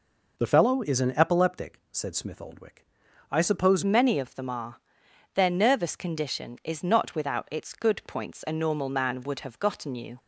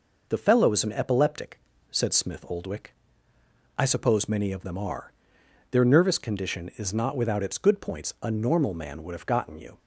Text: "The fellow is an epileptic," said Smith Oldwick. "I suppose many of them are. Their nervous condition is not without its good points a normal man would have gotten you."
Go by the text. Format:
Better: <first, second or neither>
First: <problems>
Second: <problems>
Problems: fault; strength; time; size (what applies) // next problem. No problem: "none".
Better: second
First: changes voice at "many"; from 3.8 s on; 6.3 s long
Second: none